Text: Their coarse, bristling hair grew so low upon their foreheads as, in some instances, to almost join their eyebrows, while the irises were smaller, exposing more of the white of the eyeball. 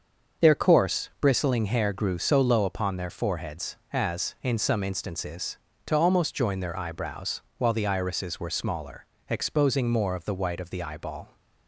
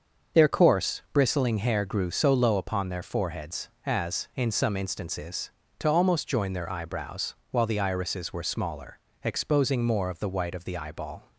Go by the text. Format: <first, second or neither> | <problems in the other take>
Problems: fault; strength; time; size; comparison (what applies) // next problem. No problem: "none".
neither | starts louder than the rest; the same in both